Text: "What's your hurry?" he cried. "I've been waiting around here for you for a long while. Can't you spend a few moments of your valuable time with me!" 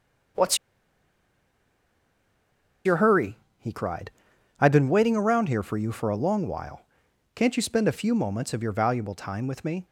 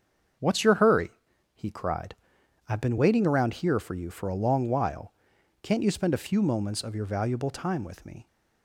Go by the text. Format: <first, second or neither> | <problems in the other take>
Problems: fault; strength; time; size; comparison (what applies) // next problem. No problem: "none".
second | starts louder than the rest; until 3.8 s; 6.5 dB; also in the second // pauses between "What's" and "your"; strong; at 0.5 s; 2.2 s long